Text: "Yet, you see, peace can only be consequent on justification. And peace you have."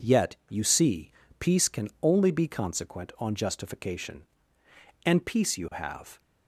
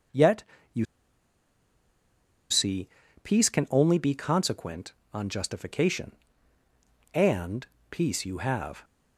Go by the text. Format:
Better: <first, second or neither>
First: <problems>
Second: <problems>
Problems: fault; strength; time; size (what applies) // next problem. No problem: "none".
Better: first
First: none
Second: pauses between "you" and "see"; strong; at 0.8 s; 1.6 s long // pauses between "And" and "peace"; slight; at 7.6 s; 0.24 s long